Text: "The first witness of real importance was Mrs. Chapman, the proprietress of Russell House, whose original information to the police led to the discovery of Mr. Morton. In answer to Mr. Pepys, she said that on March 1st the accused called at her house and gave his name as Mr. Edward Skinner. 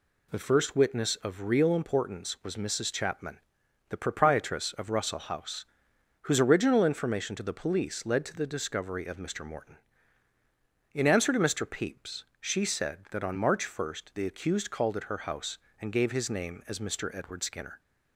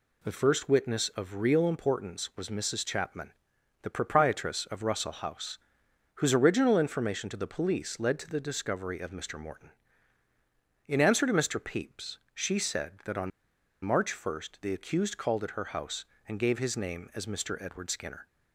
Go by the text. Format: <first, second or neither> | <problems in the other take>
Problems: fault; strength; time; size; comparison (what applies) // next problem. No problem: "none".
first | pauses between "on" and "March"; noticeable; at 13.3 s; 0.53 s long